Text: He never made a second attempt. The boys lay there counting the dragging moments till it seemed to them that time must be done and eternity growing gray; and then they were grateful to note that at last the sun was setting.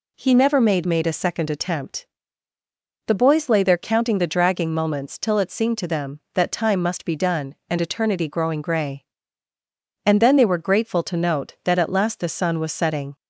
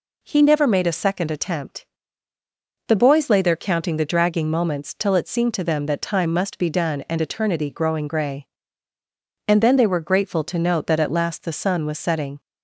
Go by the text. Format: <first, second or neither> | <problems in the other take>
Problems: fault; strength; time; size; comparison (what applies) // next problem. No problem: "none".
second | says "made" twice; at 0.8 s